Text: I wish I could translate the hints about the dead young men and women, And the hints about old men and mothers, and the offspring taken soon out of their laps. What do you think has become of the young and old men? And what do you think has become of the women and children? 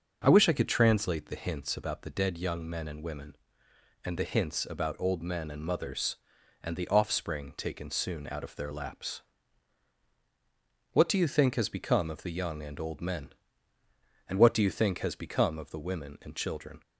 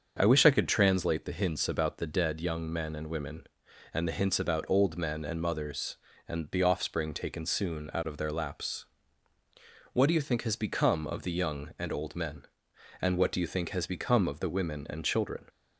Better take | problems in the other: neither | starts louder than the rest; the same in both

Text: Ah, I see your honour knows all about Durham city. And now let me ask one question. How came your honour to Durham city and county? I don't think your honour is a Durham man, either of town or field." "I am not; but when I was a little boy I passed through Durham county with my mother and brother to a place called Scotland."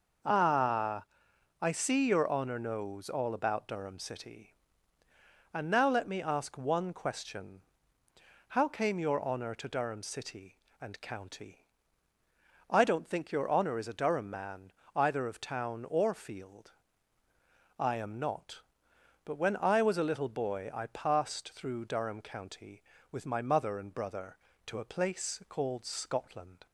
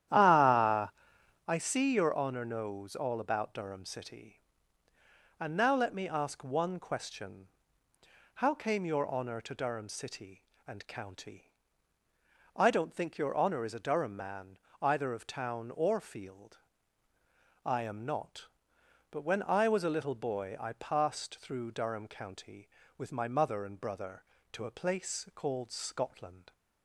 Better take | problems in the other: first | starts louder than the rest; strong; until 1.5 s; 11 dB

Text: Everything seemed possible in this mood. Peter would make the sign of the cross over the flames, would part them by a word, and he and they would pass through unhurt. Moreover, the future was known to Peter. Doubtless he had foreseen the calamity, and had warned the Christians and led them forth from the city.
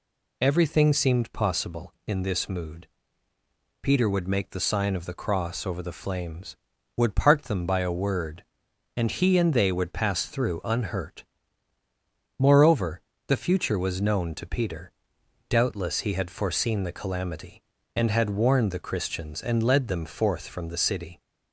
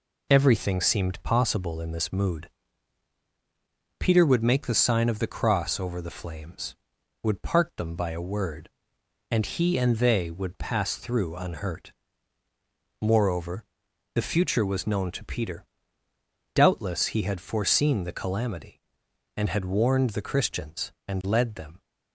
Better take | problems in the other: first | stops before "forth from the city"; at 21.8 s

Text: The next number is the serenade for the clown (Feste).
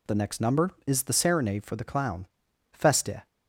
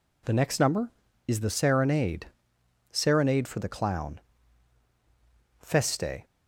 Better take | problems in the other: first | says "serenade" twice; at 2.9 s

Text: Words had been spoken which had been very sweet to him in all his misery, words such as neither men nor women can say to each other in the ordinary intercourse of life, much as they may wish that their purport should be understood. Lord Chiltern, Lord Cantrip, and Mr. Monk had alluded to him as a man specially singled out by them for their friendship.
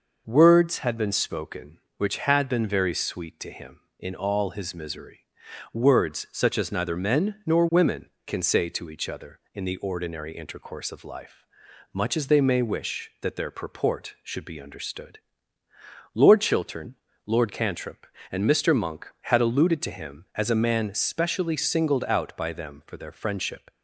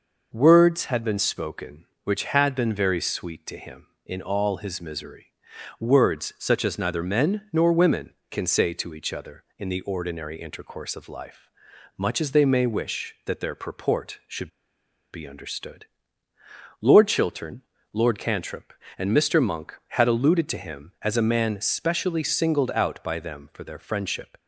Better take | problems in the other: first | pauses between "should" and "be"; noticeable; at 14.4 s; 0.63 s long

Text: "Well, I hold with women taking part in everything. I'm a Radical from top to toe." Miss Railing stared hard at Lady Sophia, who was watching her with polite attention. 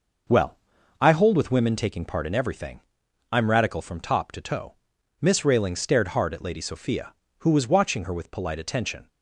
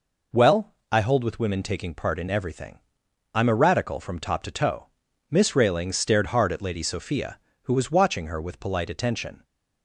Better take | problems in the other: second | skips "a"; at 3.4 s

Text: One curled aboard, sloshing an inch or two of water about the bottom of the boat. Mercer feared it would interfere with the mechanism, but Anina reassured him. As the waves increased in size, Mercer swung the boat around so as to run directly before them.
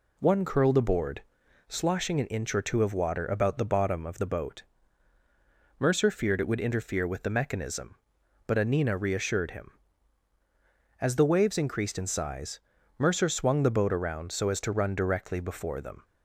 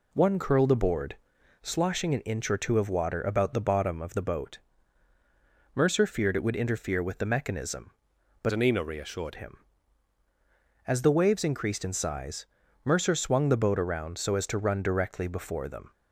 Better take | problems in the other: first | changes voice from "Anina" to "reassured"; from 8.5 to 9.3 s; 0.8 s long

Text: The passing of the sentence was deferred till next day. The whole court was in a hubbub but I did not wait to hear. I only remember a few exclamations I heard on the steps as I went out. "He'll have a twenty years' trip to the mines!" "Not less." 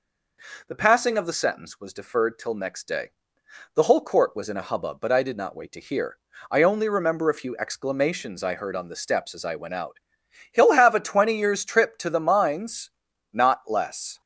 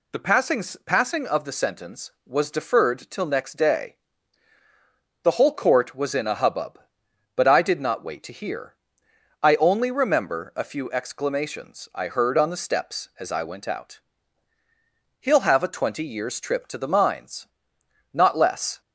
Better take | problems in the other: first | says "passing" twice; at 0.8 s

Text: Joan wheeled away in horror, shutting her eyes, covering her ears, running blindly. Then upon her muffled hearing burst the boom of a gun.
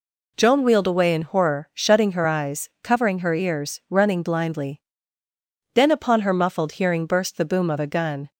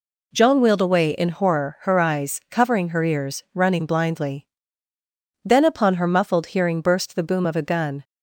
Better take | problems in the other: first | skips "shutting"; at 1.7 s

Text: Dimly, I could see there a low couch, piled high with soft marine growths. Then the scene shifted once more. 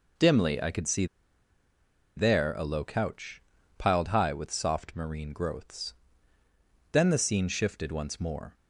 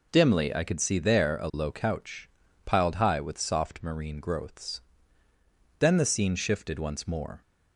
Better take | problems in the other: second | pauses between "see" and "there"; at 1.0 s; 1.1 s long

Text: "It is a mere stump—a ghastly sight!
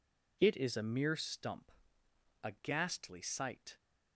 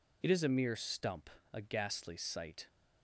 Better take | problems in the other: neither | none

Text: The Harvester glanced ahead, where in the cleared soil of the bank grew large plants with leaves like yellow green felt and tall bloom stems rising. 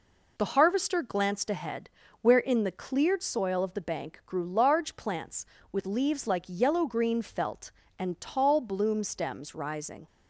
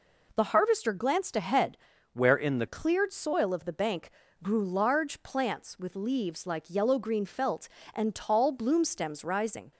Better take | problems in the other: first | changes voice from "where" to "the"; from 2.1 to 2.6 s; 0.5 s long // pauses between "bank" and "grew"; slight; at 4.0 s; 0.34 s long

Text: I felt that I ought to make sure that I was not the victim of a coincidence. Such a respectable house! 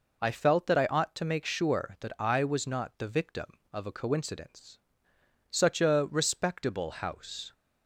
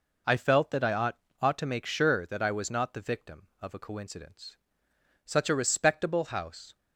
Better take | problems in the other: first | says "ought" twice; at 1.4 s

